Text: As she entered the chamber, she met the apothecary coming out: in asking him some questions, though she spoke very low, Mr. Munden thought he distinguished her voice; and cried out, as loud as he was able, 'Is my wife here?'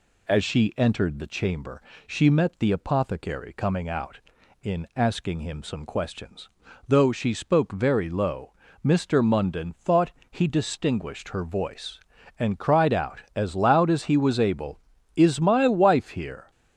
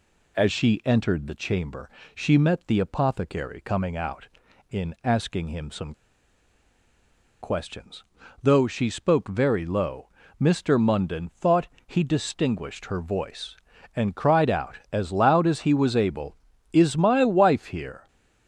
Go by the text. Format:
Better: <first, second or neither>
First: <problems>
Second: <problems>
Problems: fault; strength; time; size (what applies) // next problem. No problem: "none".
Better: first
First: pauses between "thought" and "he"; slight; at 10.1 s; 0.18 s long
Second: pauses between "some" and "questions"; strong; at 5.9 s; 1.4 s long // pauses between "thought" and "he"; slight; at 11.6 s; 0.18 s long